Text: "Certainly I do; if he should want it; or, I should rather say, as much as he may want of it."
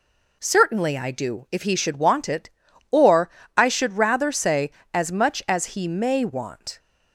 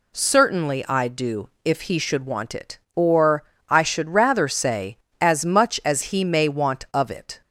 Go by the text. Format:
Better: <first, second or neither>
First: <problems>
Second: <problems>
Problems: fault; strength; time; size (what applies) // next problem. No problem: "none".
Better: second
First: stops before "of it"; at 6.7 s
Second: none